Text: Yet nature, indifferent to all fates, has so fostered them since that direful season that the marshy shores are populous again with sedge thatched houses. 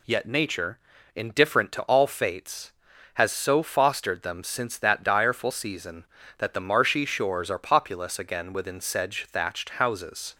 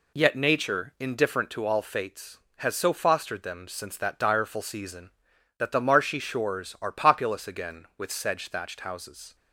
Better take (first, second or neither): second